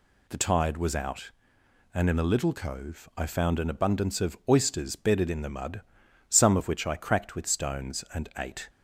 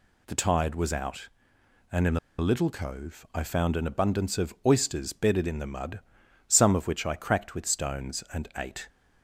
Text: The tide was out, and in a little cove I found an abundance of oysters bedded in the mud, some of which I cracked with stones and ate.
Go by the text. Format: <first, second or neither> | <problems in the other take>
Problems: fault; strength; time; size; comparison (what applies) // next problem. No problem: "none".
first | pauses between "in" and "a"; slight; at 2.1 s; 0.21 s long